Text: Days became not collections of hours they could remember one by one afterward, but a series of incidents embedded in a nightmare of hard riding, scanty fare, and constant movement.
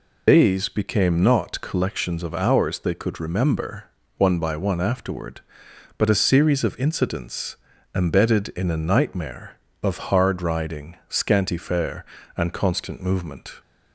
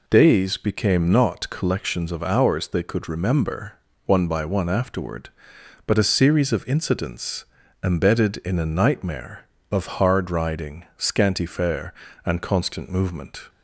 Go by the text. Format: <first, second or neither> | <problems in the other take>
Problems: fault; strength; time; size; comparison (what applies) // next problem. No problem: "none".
second | loses the start of "Days"; at 0.2 s; 85 ms // pauses between "remember" and "one"; slight; at 3.8 s; 0.34 s long; slight in the second // pauses between "incidents" and "embedded"; at 7.5 s; 0.38 s long; also in the second